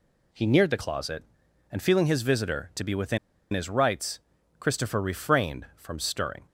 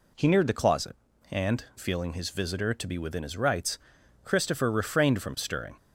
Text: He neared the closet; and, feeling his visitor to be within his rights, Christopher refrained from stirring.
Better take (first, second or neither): second